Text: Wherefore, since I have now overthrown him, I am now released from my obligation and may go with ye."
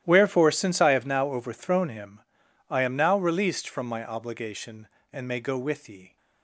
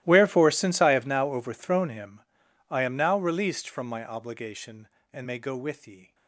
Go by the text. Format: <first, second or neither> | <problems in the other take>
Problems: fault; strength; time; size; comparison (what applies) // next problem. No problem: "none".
first | gets quieter; strong; throughout; 21 dB // starts louder than the rest; strong; until 1.0 s; 16 dB; strong in the first